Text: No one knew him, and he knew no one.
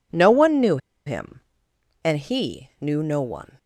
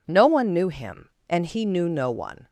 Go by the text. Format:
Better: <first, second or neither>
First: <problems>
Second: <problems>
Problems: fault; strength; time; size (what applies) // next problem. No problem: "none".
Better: second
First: pauses between "knew" and "him"; slight; at 0.7 s; 0.28 s long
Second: none